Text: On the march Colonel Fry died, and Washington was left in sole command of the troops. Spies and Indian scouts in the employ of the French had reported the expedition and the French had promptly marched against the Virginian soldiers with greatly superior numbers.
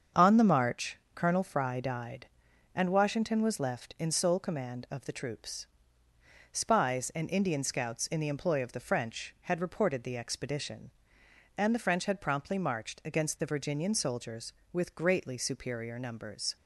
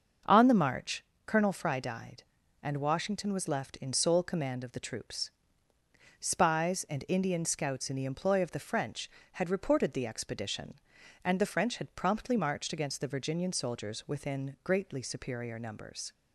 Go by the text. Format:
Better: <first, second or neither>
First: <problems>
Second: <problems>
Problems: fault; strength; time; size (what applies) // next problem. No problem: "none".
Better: first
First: starts louder than the rest; until 1.3 s; 7 dB // pauses between "march" and "Colonel"; slight; at 0.9 s; 0.18 s long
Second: starts louder than the rest; until 1.4 s; 6.5 dB // pauses between "march" and "Colonel"; slight; at 1.0 s; 0.22 s long // says "within" for "with"; at 14.0 s